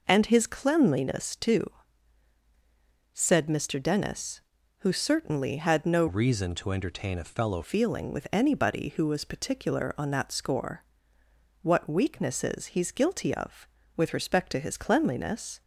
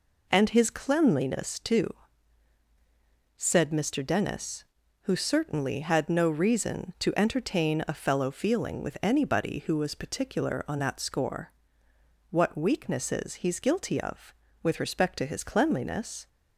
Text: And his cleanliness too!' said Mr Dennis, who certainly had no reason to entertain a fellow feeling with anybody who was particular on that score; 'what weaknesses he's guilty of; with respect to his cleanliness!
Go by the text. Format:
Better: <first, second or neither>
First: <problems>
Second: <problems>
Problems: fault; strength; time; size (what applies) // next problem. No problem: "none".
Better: second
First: changes voice from "reason" to "fellow"; from 6.0 to 7.6 s; 1.6 s long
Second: none